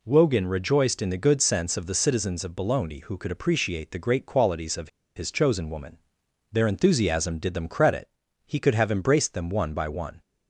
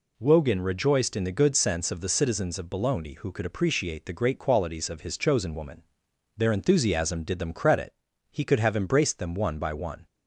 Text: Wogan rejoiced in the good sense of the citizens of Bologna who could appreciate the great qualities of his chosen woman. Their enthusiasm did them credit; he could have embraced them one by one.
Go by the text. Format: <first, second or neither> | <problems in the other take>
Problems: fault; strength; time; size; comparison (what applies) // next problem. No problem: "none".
second | pauses between "of" and "his"; slight; at 4.8 s; 0.27 s long